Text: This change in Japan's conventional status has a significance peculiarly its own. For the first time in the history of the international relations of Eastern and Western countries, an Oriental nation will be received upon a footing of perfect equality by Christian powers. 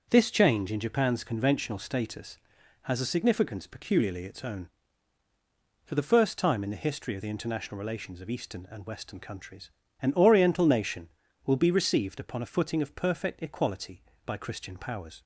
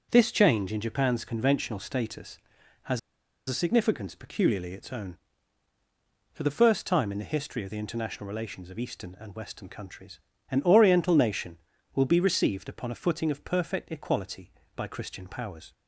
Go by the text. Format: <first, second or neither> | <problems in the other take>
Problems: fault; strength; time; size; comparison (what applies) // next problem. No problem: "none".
first | starts louder than the rest; until 1.1 s; 6.5 dB; also in the first // pauses between "has" and "a"; noticeable; at 2.9 s; 0.50 s long